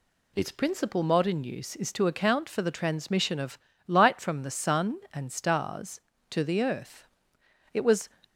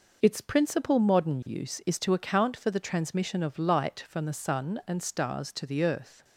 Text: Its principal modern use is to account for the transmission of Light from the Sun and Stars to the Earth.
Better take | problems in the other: second | pauses between "of" and "Light"; slight; at 3.5 s; 0.28 s long // goes on to say "It was"; slight; from 7.7 s on; 0.36 s long

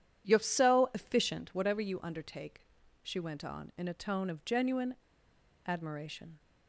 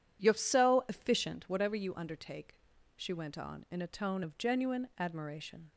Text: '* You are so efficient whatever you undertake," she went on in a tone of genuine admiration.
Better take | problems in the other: second | pauses between "genuine" and "admiration"; noticeable; at 4.9 s; 0.71 s long

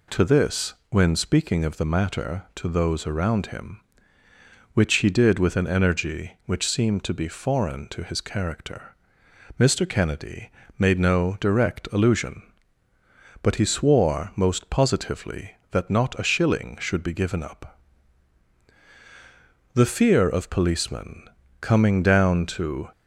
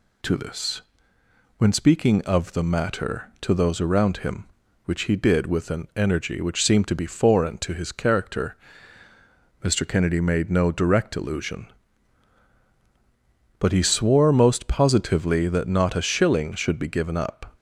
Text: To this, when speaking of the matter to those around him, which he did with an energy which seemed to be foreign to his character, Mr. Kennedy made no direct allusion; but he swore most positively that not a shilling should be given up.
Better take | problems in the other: second | pauses between "Kennedy" and "made"; slight; at 10.4 s; 0.30 s long // goes on to say "The fear of policemen coming down to"; strong; from 19.7 s on; 3.1 s long

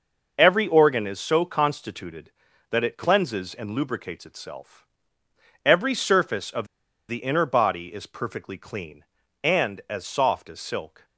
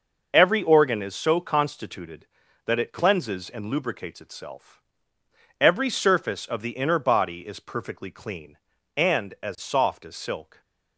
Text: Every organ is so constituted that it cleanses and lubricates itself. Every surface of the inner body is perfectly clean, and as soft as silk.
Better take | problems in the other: second | pauses between "of" and "the"; at 6.6 s; 0.44 s long

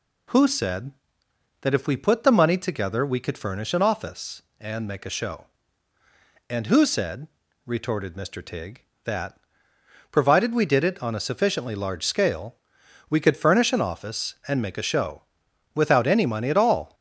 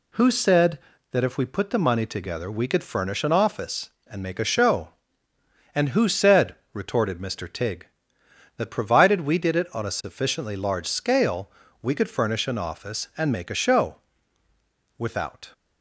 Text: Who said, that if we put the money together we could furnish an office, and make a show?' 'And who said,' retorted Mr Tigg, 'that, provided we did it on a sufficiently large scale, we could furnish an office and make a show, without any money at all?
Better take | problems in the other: first | stops before "any money at all"; at 15.5 s

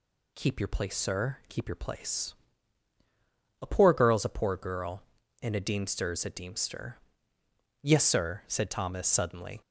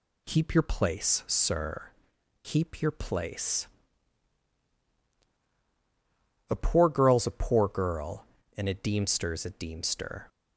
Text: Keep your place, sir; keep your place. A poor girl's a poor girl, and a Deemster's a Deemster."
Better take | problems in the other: second | goes on to say "Yes sir said Thomas suddenly"; strong; from 7.8 s on; 1.7 s long

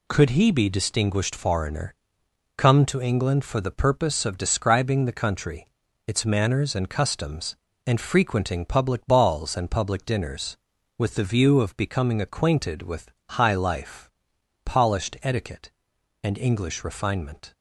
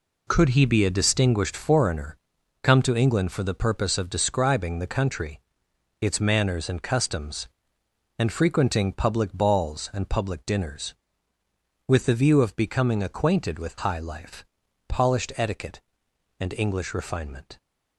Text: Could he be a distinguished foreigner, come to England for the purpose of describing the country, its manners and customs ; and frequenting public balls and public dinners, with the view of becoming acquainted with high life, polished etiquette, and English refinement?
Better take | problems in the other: second | skips "a"; at 0.6 s // pauses between "with" and "high"; slight; at 13.1 s; 0.18 s long

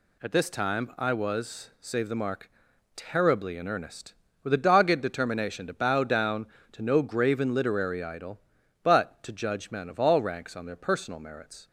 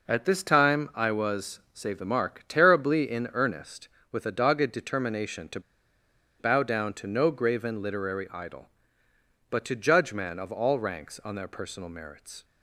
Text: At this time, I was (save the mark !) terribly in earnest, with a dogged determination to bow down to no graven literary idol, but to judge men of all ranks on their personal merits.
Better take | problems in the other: first | pauses between "to" and "bow"; noticeable; at 5.5 s; 0.79 s long

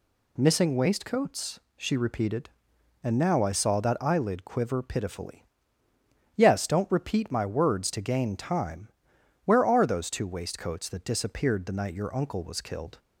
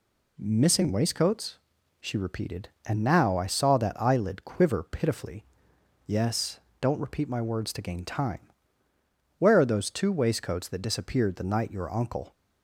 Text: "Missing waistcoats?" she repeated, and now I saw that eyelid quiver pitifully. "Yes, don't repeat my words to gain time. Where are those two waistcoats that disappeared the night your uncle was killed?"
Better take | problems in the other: first | stops before "was killed"; at 12.3 s

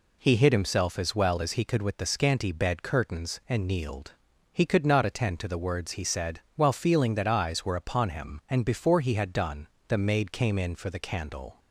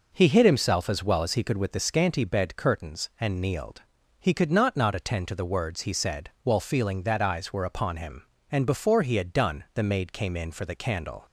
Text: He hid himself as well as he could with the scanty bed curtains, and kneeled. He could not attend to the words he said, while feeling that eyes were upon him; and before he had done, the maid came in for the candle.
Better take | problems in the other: first | says "not" twice; at 4.7 s

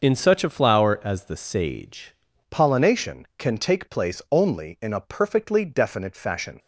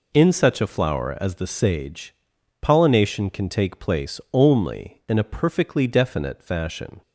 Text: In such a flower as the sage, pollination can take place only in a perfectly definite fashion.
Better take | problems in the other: second | starts louder than the rest; noticeable; until 1.0 s; 6 dB // changes voice at "pollination"; from 2.5 s on; 4.0 s long

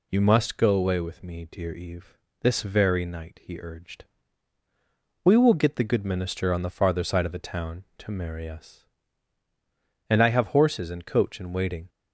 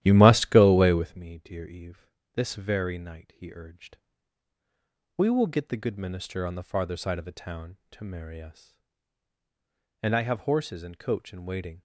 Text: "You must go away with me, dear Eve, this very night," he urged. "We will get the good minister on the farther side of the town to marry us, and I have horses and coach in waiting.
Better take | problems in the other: first | starts louder than the rest; strong; until 1.2 s; 13 dB

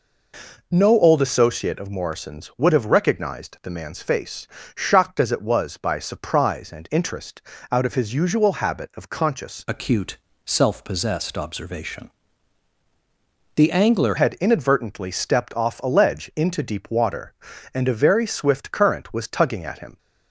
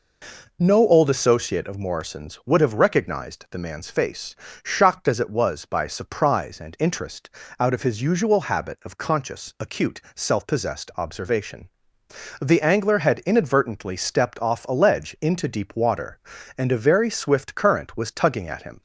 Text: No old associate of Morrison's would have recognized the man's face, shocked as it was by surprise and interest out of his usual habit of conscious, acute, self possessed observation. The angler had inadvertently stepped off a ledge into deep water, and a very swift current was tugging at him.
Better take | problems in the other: second | pauses between "interest" and "out"; slight; at 7.4 s; 0.30 s long; slight in the second // changes voice from "acute" to "angler"; from 9.6 to 14.1 s; 4.5 s long

